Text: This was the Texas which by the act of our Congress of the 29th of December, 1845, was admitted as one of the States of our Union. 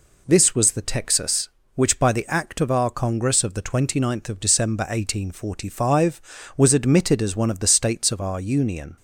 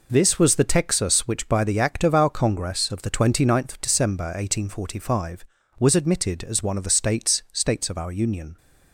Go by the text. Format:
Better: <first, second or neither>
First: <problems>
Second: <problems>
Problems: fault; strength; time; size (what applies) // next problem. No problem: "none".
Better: first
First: none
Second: says "States" twice; at 7.5 s